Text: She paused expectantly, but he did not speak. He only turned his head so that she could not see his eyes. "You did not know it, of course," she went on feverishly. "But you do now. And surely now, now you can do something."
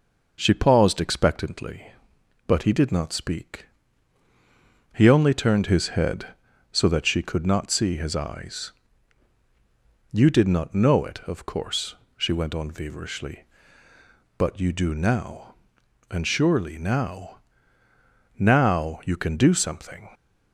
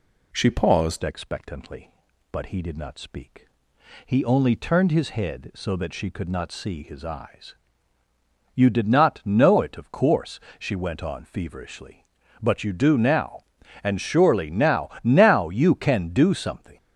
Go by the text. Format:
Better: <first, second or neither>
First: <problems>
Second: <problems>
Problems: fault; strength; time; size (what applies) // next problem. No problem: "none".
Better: first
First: none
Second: changes voice at "expectantly"; from 1.0 s on; 15.7 s long